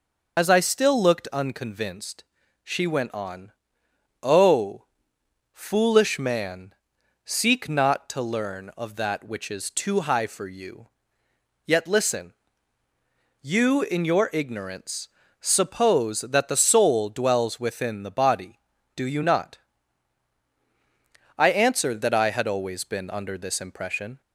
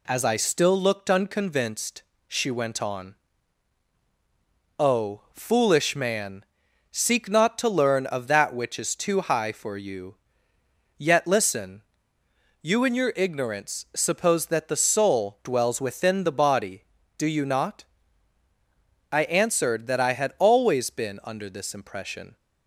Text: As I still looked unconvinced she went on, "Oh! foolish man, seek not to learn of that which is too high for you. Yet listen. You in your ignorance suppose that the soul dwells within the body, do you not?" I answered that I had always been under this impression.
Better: second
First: loses the start of "As"; at 0.3 s; 40 ms // pauses between "unconvinced" and "she"; at 2.2 s; 0.40 s long // pauses between "ignorance" and "suppose"; slight; at 15.0 s; 0.32 s long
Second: pauses between "unconvinced" and "she"; slight; at 2.0 s; 0.26 s long

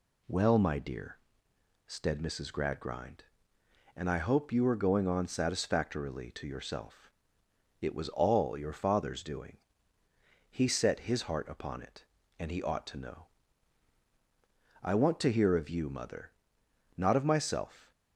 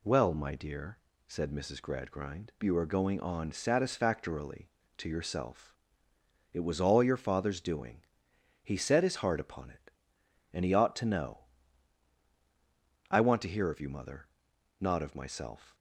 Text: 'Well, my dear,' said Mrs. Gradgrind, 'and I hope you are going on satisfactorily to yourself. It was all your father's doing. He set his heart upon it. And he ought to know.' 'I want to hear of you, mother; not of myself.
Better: first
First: none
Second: skips "and I hope"; at 2.5 s

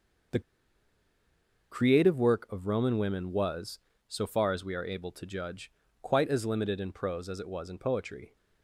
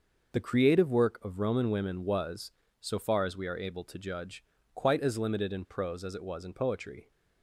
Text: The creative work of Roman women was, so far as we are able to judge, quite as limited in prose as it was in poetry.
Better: second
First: pauses between "The" and "creative"; strong; at 0.4 s; 1.3 s long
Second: none

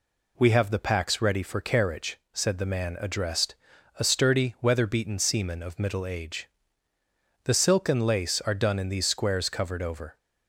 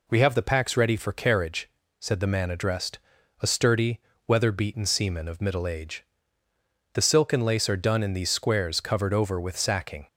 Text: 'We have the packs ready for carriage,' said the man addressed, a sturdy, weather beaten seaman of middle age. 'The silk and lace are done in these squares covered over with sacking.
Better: second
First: stops before "with sacking"; at 10.1 s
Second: none

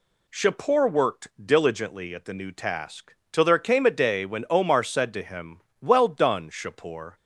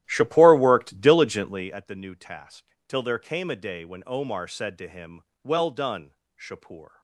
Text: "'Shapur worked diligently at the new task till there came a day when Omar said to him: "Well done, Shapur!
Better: first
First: pauses between "task" and "till"; slight; at 3.1 s; 0.16 s long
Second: starts louder than the rest; strong; until 1.9 s; 13 dB // pauses between "task" and "till"; slight; at 2.6 s; 0.24 s long

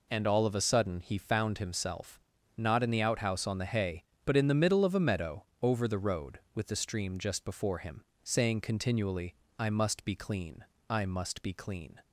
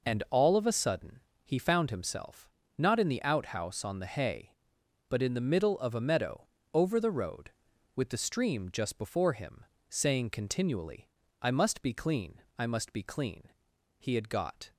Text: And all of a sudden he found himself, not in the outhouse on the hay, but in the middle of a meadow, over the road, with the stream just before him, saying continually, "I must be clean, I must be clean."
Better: first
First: none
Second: pauses between "sudden" and "he"; slight; at 1.1 s; 0.24 s long // goes on to say "He had got"; noticeable; from 13.9 s on; 0.76 s long

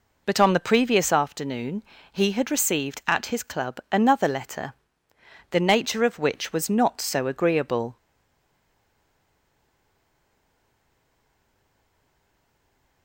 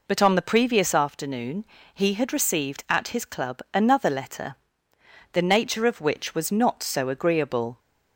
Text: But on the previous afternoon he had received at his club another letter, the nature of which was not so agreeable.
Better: second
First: pauses between "afternoon" and "he"; slight; at 1.8 s; 0.30 s long // stays silent after the last word; strong; from 7.9 s on; 5.1 s long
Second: pauses between "afternoon" and "he"; slight; at 1.6 s; 0.30 s long

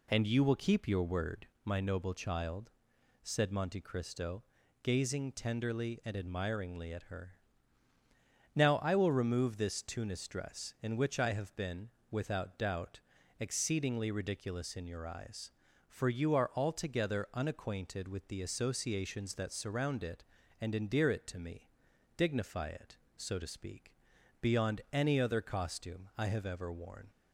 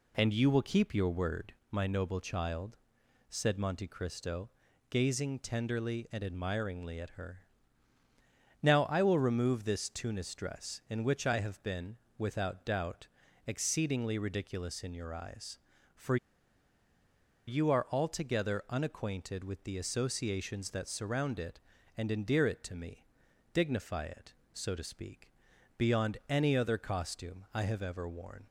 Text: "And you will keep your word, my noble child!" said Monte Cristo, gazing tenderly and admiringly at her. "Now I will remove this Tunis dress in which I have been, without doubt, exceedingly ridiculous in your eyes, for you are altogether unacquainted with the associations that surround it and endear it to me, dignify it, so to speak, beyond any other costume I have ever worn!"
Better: first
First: none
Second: pauses between "for" and "you"; strong; at 16.1 s; 1.3 s long

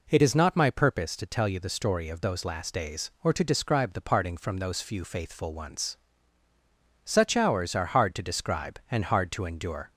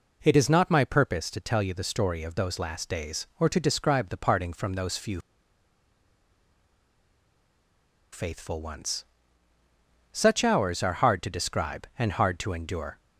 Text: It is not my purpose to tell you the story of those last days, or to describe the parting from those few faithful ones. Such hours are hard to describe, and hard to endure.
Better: first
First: none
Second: pauses between "few" and "faithful"; strong; at 5.1 s; 2.9 s long

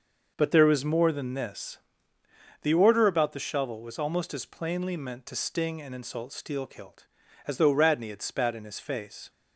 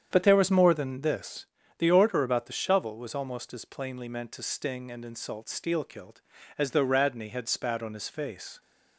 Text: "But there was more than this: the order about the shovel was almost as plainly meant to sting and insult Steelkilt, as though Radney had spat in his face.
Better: first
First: none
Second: starts louder than the rest; strong; until 1.1 s; 8.5 dB // says "on" for "in"; at 7.8 s

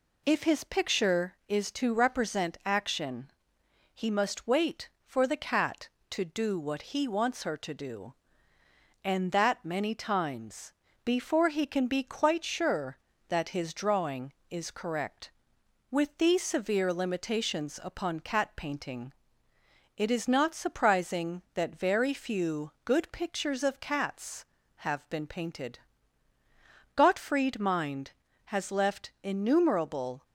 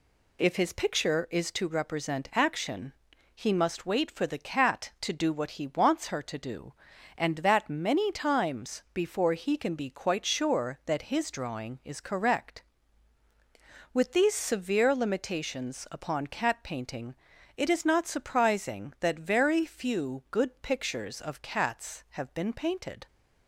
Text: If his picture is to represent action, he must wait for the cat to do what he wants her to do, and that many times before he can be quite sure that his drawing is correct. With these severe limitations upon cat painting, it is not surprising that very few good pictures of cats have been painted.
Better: second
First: pauses between "times" and "before"; slight; at 10.7 s; 0.32 s long // pauses between "few" and "good"; slight; at 22.7 s; 0.16 s long // goes on to say "Gottfried Mind has left innumerable"; strong; from 26.9 s on; 3.3 s long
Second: none

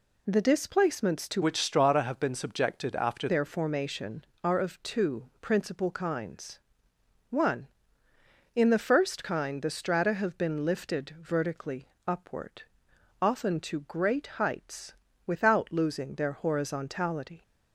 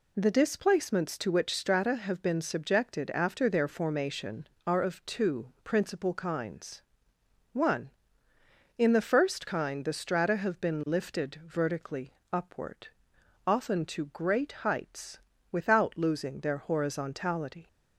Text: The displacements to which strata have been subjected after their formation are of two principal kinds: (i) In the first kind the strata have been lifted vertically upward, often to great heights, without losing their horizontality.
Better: second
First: changes voice from "which" to "after"; from 1.4 to 3.2 s; 1.8 s long // pauses between "vertically" and "upward"; slight; at 11.8 s; 0.18 s long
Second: pauses between "vertically" and "upward"; slight; at 12.1 s; 0.18 s long

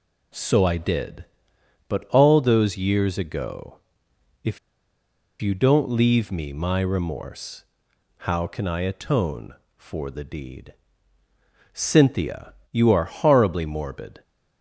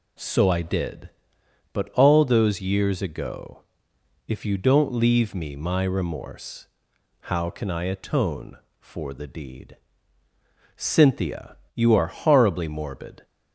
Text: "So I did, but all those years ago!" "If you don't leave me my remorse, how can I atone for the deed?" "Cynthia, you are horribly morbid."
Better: second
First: pauses between "If" and "you"; noticeable; at 4.5 s; 0.83 s long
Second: none

